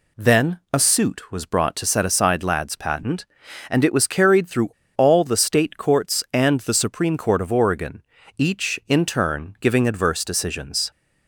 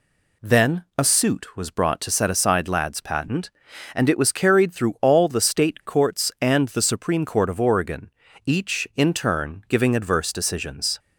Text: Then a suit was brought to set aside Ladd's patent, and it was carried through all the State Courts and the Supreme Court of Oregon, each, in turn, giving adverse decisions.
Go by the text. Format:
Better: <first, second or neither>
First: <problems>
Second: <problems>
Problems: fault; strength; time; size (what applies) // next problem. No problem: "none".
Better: second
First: pauses between "through" and "all"; slight; at 4.6 s; 0.26 s long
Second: none